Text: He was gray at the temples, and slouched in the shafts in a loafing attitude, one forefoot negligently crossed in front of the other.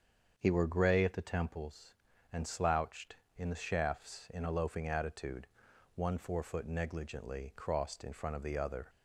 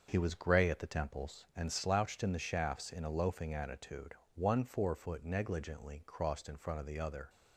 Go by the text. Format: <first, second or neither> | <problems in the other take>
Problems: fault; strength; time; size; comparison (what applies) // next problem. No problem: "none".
second | starts louder than the rest; until 1.3 s; 7 dB; also in the second // says "were" for "was"; at 0.5 s